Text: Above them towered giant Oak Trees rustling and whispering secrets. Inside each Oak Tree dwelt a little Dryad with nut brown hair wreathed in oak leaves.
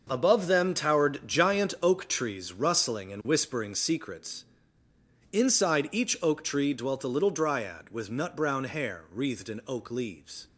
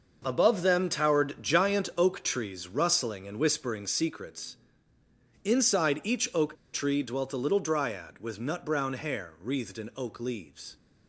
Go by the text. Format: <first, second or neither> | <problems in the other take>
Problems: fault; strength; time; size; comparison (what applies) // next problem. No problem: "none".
first | pauses between "Oak" and "Tree"; slight; at 6.5 s; 0.17 s long